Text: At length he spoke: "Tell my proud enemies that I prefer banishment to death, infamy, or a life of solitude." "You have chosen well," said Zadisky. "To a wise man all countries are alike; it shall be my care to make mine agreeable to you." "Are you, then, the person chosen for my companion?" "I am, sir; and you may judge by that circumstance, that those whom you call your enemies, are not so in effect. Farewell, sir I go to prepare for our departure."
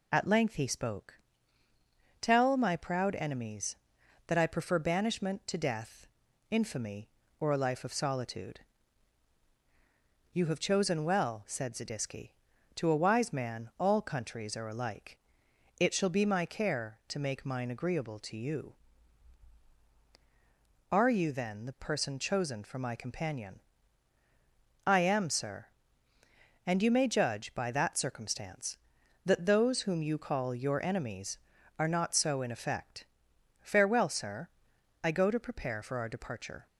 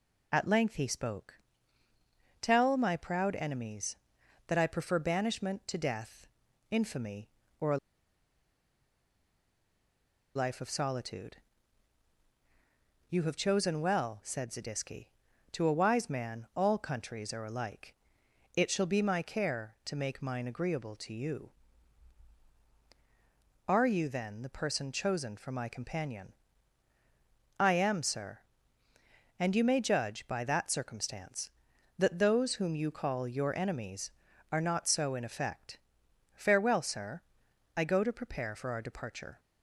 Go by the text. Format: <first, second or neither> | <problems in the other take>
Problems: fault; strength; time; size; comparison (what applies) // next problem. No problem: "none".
first | pauses between "a" and "life"; strong; at 7.7 s; 2.5 s long // pauses between "sir" and "I"; noticeable; at 37.2 s; 0.56 s long; noticeable in the first